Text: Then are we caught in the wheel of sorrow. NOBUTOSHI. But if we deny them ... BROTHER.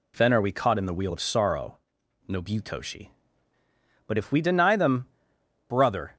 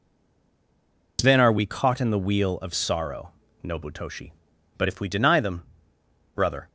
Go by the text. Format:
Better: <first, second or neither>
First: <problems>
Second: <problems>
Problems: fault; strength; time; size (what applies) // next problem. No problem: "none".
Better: first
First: none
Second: stays silent before the first word; noticeable; until 1.1 s; 1.1 s long